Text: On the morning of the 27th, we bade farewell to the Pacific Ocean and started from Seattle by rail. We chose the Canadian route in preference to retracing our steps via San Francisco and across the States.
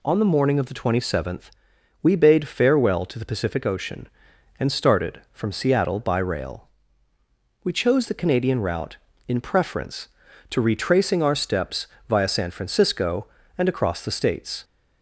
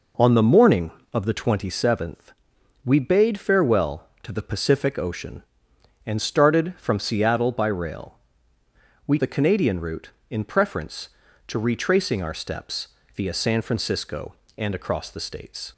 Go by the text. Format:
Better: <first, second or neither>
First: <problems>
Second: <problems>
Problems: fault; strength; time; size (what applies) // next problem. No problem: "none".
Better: first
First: pauses between "steps" and "via"; slight; at 11.8 s; 0.22 s long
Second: skips "chose"; at 9.1 s // pauses between "steps" and "via"; slight; at 12.8 s; 0.24 s long